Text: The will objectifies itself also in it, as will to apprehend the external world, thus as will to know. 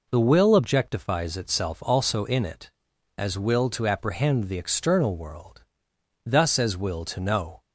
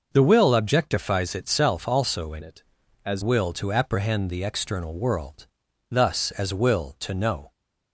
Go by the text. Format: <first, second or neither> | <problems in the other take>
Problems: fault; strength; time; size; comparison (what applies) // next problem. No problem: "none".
first | changes voice from "it" to "as"; from 2.4 to 3.2 s; 0.8 s long